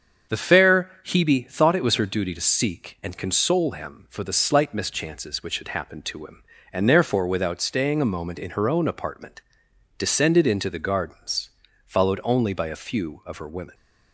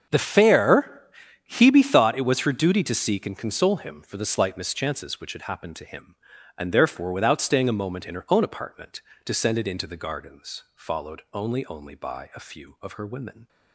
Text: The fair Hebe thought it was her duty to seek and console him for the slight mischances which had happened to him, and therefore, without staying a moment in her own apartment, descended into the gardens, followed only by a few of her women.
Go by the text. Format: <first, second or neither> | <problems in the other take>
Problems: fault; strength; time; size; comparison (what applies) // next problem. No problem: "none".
first | starts louder than the rest; until 1.5 s; 7 dB; also in the first // pauses between "fair" and "Hebe"; noticeable; at 1.0 s; 0.48 s long // says "only" twice; at 11.6 s